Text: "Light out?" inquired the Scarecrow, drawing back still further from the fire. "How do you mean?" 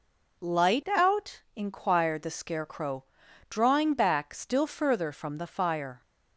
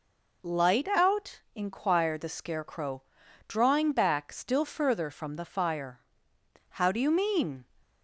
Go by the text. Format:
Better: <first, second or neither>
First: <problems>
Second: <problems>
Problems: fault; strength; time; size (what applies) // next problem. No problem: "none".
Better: second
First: stops before "How do you mean"; at 6.0 s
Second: none